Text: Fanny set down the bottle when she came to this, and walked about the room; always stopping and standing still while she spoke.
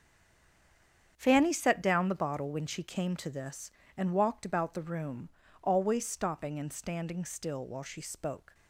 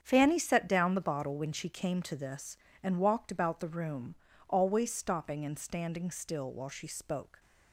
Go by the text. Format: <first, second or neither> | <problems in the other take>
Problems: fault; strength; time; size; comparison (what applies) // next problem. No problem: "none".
second | stays silent before the first word; noticeable; until 1.1 s; 1.1 s long // starts louder than the rest; strong; until 2.1 s; 8 dB; strong in the second